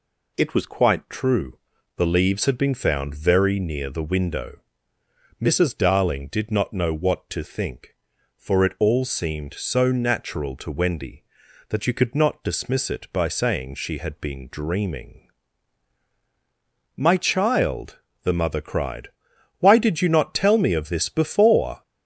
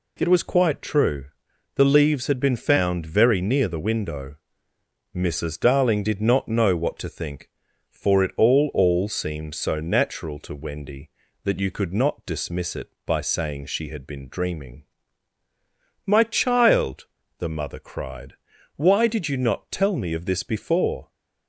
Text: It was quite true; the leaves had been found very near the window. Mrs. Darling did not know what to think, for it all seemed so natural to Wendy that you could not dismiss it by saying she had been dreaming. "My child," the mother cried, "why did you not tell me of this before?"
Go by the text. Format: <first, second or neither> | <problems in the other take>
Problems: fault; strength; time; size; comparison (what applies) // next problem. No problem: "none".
first | says "all" twice; at 8.7 s